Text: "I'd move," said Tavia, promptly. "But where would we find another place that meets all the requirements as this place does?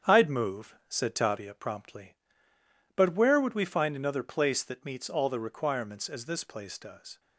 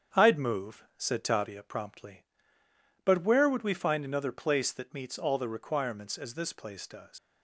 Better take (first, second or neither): first